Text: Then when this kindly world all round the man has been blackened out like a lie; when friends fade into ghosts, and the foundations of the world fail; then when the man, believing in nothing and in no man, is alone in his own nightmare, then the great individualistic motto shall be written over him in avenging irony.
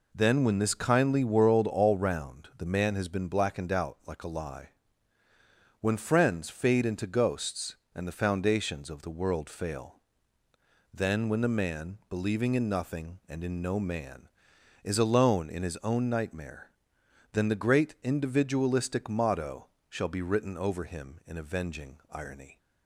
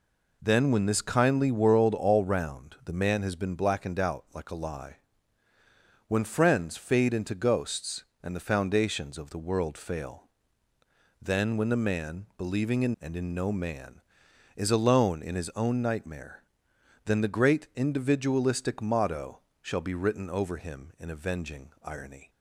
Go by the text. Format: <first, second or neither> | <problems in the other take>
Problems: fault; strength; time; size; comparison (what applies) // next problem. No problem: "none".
first | skips "nothing"; at 12.9 s // pauses between "motto" and "shall"; slight; at 19.3 s; 0.20 s long; slight in the first